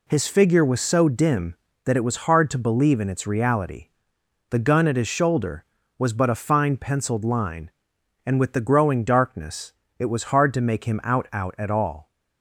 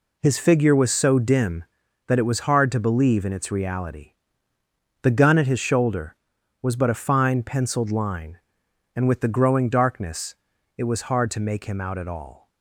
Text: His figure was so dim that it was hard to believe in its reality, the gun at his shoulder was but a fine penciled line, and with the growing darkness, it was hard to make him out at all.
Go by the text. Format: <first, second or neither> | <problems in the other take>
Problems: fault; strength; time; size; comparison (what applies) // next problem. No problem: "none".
second | says "out" twice; at 11.3 s